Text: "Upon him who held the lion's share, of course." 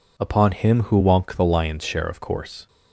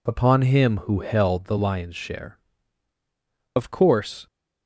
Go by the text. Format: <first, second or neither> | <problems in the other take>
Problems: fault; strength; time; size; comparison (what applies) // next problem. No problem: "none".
second | says "wonk" for "held"; at 0.9 s